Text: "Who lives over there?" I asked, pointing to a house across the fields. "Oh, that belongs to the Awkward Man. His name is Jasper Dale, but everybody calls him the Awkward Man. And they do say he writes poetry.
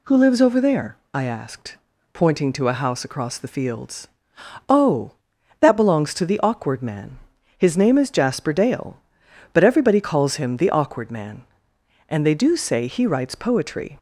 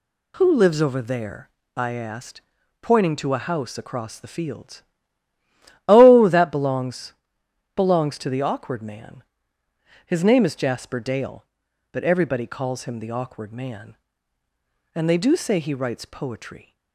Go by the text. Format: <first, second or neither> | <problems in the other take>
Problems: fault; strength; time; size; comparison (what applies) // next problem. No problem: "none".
first | says "belongs" twice; at 7.7 s